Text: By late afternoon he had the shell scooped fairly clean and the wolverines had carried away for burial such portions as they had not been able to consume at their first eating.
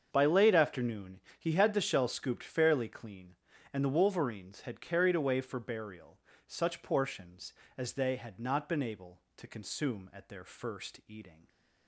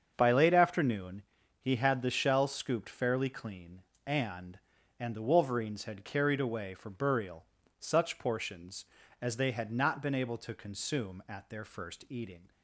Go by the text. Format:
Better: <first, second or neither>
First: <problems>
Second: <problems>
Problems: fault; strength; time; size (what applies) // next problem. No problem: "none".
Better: first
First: starts louder than the rest; until 1.1 s; 7 dB // pauses between "afternoon" and "he"; slight; at 1.2 s; 0.18 s long // pauses between "burial" and "such"; slight; at 6.1 s; 0.28 s long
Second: starts louder than the rest; until 1.1 s; 7 dB // pauses between "afternoon" and "he"; slight; at 1.2 s; 0.36 s long // says "and" twice; at 4.9 s // pauses between "burial" and "such"; slight; at 7.4 s; 0.34 s long